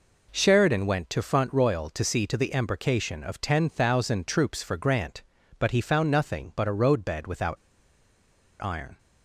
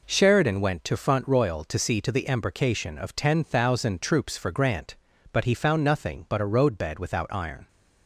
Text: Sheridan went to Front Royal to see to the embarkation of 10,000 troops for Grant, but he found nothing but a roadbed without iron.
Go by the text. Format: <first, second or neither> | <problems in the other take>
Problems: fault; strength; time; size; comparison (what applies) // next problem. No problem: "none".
second | pauses between "without" and "iron"; at 7.5 s; 1.0 s long